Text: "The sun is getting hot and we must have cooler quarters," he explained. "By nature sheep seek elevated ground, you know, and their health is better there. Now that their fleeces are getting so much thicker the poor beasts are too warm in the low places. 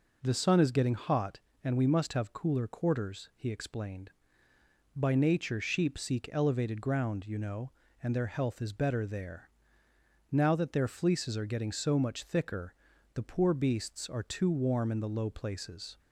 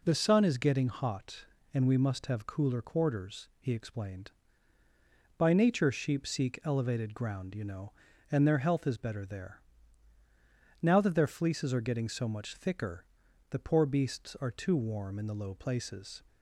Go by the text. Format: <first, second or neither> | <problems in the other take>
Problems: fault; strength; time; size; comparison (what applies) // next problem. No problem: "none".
neither | pauses between "thicker" and "the"; the same in both